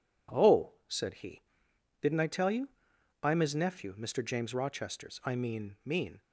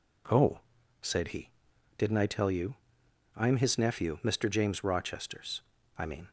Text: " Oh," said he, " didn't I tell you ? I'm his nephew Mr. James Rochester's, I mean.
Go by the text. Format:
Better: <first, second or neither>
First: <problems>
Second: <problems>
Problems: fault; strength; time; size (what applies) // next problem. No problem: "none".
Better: second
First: says "mean" twice; at 5.8 s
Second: none